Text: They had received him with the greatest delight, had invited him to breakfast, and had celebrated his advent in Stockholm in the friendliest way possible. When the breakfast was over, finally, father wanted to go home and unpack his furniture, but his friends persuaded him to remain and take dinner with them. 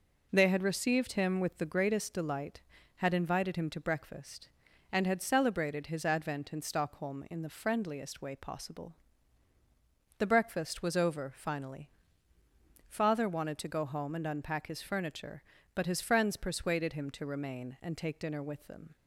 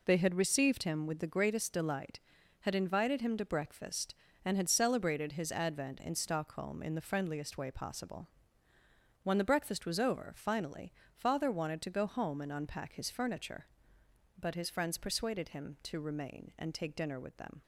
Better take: second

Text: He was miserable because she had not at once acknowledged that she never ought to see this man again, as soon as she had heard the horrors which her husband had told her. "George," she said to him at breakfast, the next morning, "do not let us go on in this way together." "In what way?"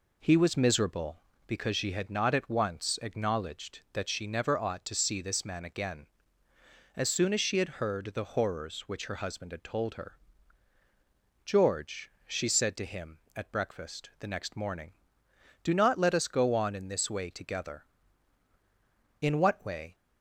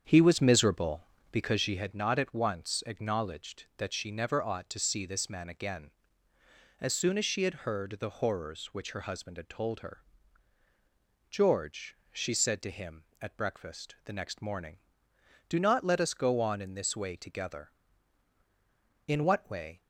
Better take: first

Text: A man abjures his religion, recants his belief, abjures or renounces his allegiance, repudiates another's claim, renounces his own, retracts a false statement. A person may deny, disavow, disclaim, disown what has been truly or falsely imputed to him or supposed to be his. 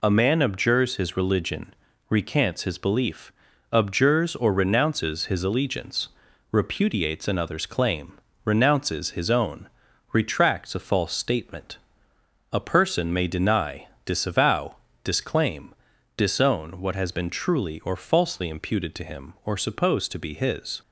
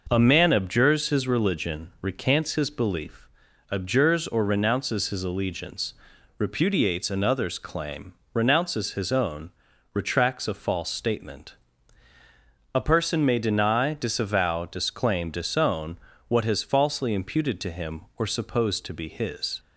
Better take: first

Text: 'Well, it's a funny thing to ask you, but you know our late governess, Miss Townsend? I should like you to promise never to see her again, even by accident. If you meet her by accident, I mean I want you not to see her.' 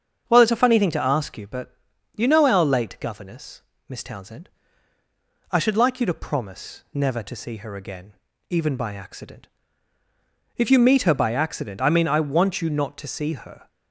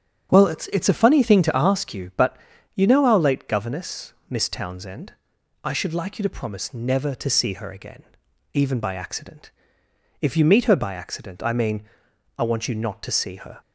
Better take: first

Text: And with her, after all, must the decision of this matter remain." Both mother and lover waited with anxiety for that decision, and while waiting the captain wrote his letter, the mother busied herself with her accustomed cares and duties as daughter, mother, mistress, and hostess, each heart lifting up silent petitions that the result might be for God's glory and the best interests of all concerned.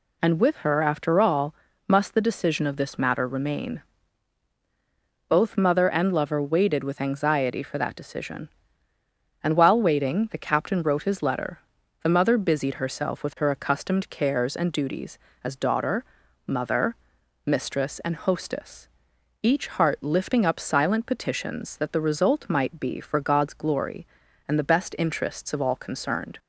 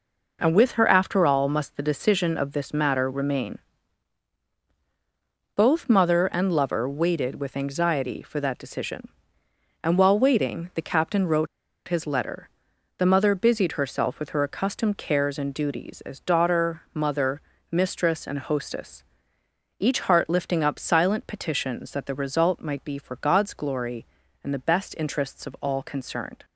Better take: first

